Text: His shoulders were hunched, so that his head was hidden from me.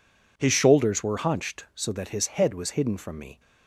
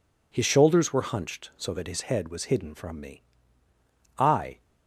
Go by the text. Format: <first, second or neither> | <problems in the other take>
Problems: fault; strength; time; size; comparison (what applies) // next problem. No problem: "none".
first | goes on to say "I"; slight; from 4.1 s on; 0.44 s long